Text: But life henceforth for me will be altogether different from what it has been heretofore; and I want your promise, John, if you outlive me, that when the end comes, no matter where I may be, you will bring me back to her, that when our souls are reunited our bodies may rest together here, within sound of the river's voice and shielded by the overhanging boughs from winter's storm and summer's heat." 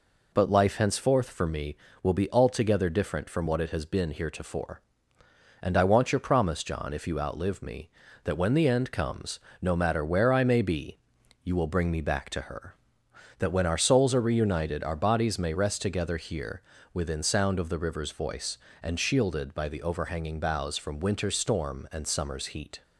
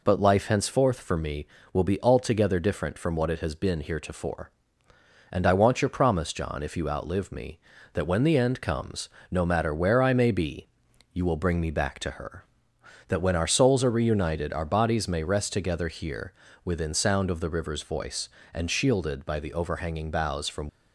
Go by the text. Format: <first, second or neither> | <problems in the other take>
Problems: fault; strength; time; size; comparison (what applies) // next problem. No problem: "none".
first | stops before "winter's storm and summer's heat"; at 20.6 s